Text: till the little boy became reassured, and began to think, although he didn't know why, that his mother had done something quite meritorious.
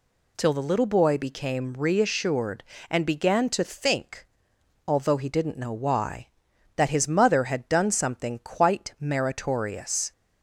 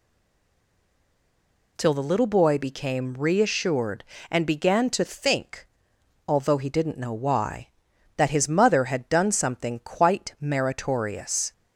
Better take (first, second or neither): first